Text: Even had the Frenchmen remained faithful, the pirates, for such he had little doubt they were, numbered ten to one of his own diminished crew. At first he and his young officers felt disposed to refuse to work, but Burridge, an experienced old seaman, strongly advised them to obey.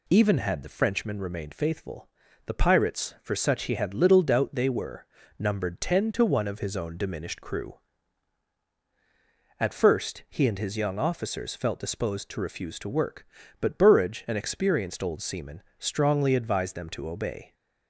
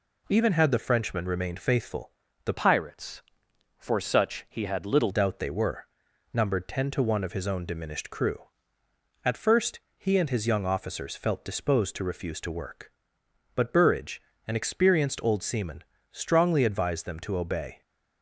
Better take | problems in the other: first | changes voice from "pirates" to "little"; from 2.5 to 5.0 s; 2.5 s long // pauses between "first" and "he"; slight; at 9.7 s; 0.16 s long

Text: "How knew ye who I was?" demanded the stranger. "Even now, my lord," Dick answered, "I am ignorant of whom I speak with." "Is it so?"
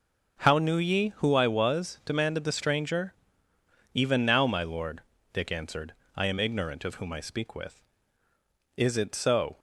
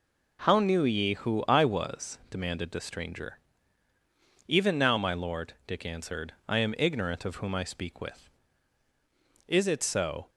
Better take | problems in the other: neither | none

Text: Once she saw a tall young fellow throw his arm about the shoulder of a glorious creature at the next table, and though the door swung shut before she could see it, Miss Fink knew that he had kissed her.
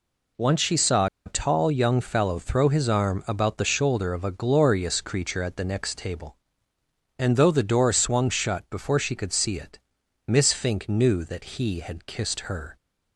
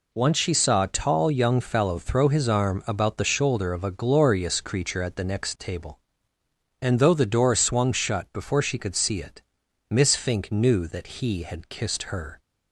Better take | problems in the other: second | pauses between "saw" and "a"; slight; at 1.0 s; 0.18 s long

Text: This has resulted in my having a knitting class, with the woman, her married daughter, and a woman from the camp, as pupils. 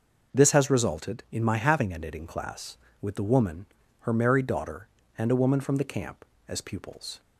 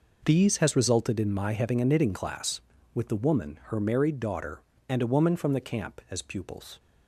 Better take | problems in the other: first | says "These" for "This"; at 0.2 s

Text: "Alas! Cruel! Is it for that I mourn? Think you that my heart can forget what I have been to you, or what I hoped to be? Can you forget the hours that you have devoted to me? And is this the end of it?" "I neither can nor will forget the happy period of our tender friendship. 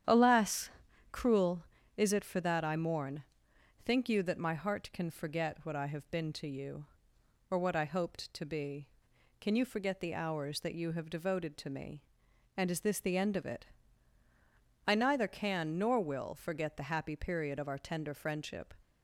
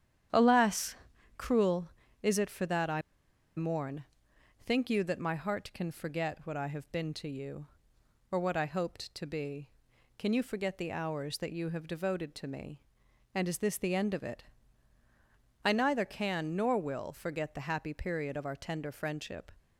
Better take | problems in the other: first | starts louder than the rest; strong; until 1.7 s; 10 dB; strong in the first // pauses between "I" and "mourn"; noticeable; at 3.0 s; 0.56 s long

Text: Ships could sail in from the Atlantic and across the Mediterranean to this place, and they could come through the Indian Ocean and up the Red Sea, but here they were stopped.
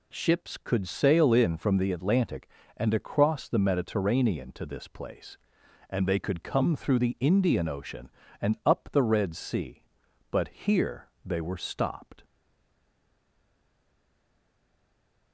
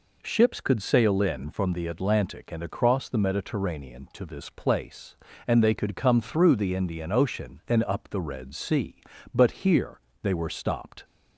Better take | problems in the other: second | pauses between "here" and "they"; slight; at 11.0 s; 0.16 s long; slight in the second // stays silent after the last word; strong; from 12.2 s on; 3.1 s long

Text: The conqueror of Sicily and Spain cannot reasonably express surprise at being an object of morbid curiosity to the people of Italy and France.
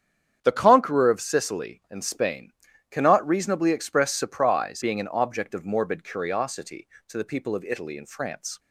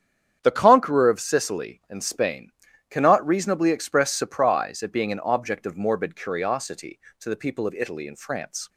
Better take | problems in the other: second | starts louder than the rest; strong; until 1.4 s; 8.5 dB; strong in the second // pauses between "Spain" and "cannot"; at 2.5 s; 0.38 s long; also in the second // skips "at"; at 4.8 s

